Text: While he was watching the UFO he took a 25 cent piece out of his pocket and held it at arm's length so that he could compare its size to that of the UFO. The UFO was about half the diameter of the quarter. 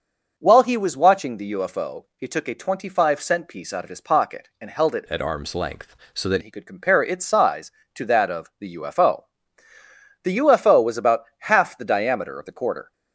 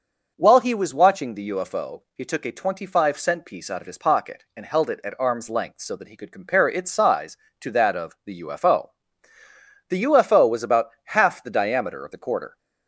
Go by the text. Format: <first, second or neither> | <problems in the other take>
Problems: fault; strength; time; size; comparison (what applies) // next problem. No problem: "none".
second | changes voice from "at" to "that"; from 5.0 to 6.4 s; 1.4 s long // pauses between "about" and "half"; slight; at 11.2 s; 0.16 s long; slight in the second